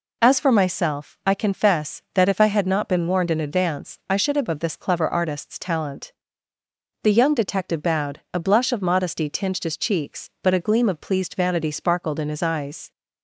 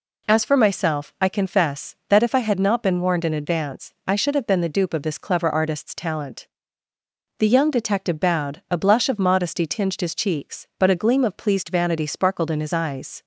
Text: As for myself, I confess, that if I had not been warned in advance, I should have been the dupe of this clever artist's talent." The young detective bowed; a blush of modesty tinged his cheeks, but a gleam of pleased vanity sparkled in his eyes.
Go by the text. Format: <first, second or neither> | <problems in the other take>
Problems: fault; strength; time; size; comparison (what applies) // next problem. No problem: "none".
second | skips "been the dupe"; at 4.4 s